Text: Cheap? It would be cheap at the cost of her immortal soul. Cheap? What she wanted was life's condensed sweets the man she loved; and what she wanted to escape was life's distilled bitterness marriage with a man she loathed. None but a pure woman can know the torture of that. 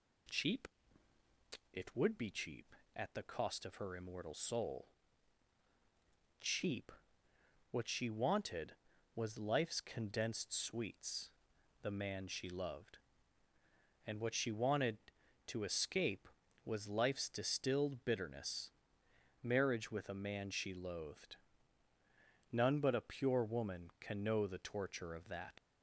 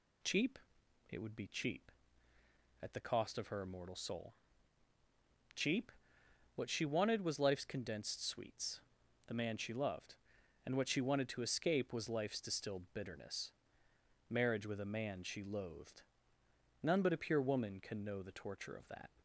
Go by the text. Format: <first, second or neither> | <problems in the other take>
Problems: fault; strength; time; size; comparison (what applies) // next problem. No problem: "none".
second | pauses between "sweets" and "the"; noticeable; at 11.2 s; 0.52 s long; noticeable in the second // pauses between "bitterness" and "marriage"; noticeable; at 18.6 s; 0.72 s long; noticeable in the second // leaves "that" unfinished; at 25.5 s; 95 ms